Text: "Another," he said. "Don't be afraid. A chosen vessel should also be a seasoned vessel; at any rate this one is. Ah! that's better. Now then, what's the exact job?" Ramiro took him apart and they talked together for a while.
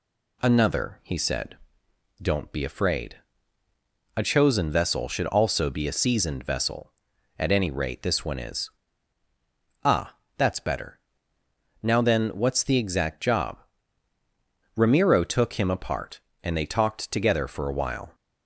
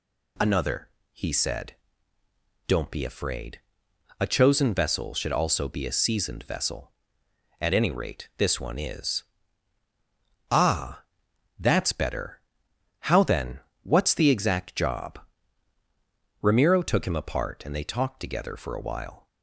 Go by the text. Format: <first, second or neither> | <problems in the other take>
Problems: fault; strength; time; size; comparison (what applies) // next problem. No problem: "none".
first | says "How" for "Now"; at 12.9 s